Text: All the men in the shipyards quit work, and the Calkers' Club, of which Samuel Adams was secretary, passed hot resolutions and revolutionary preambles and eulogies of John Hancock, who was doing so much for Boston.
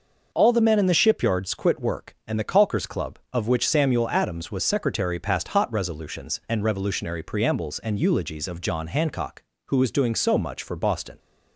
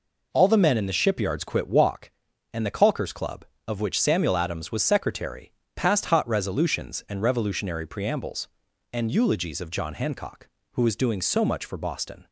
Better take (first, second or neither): first